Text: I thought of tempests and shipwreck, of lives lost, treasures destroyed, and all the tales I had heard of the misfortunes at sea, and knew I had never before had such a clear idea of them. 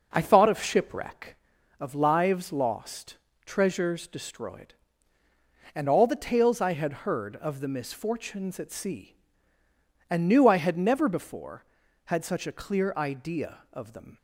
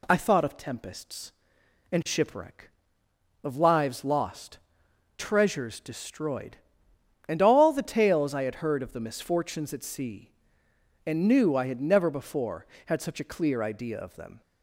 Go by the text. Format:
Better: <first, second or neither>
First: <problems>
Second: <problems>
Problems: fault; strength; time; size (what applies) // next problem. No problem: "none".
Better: second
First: skips "tempests and"; at 0.6 s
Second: none